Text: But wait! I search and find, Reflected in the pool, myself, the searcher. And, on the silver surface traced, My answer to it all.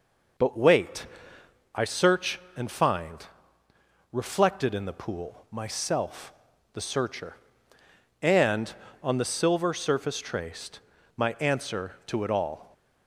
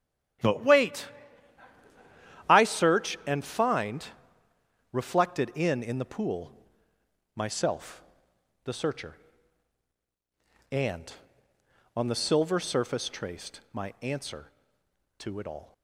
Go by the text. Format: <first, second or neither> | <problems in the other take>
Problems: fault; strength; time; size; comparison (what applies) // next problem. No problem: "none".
first | starts louder than the rest; strong; until 2.8 s; 11.5 dB // says "in" twice; at 5.8 s